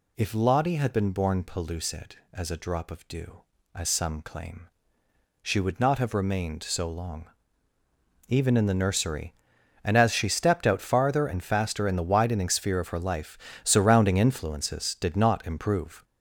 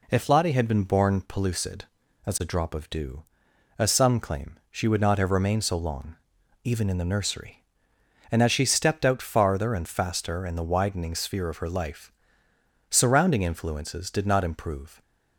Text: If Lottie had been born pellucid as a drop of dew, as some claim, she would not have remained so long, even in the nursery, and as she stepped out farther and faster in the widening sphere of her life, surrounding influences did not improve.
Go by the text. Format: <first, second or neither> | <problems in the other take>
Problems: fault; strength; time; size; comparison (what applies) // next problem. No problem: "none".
second | gets louder; throughout; 6.5 dB